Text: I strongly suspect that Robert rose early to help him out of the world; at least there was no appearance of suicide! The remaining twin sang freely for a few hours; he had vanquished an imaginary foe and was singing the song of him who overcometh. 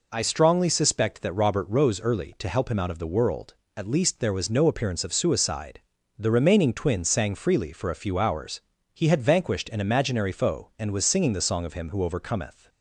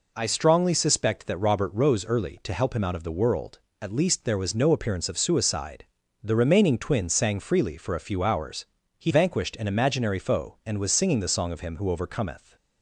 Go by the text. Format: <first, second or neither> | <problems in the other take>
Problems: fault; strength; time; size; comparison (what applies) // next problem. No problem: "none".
first | skips "had"; at 9.1 s